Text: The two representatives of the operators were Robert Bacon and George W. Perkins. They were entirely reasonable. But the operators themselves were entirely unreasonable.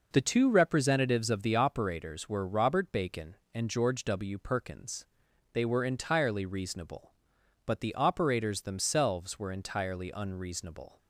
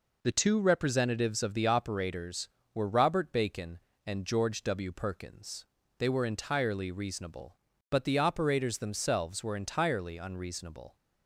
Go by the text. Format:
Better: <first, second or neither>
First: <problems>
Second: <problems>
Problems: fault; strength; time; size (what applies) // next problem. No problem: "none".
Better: neither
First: none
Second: none